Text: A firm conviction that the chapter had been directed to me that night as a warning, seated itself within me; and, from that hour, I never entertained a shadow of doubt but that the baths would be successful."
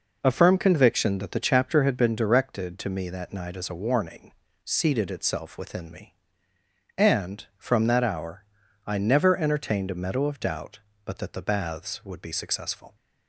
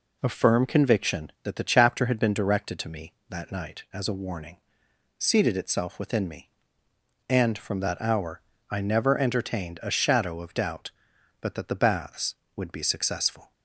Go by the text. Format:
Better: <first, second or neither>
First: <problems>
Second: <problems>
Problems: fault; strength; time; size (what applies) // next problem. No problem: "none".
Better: second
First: says "meadow" for "shadow"; at 9.9 s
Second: none